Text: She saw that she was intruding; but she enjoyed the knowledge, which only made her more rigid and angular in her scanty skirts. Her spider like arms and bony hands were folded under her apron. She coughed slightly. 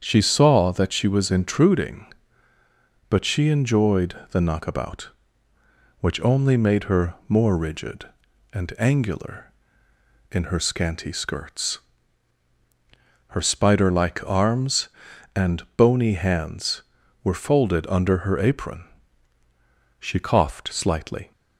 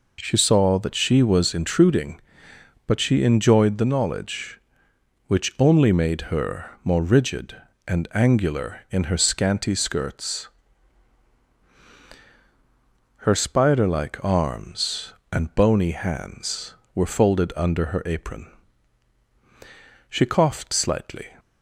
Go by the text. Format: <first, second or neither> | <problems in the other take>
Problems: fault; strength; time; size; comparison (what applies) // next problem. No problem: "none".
second | starts louder than the rest; strong; until 1.0 s; 7.5 dB // pauses between "enjoyed" and "the"; slight; at 4.1 s; 0.16 s long // says "knockabout" for "knowledge"; at 4.4 s // pauses between "her" and "more"; slight; at 7.1 s; 0.16 s long